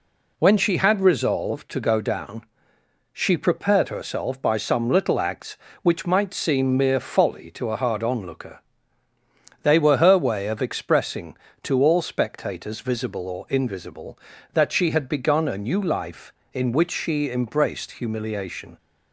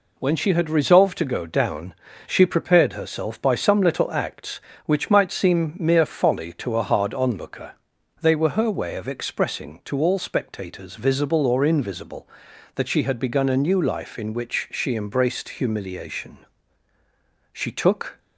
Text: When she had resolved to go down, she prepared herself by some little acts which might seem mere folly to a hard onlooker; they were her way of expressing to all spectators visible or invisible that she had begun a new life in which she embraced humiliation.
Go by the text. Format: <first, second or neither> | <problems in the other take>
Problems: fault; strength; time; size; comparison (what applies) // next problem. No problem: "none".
first | goes on to say "She took"; noticeable; from 17.5 s on; 0.66 s long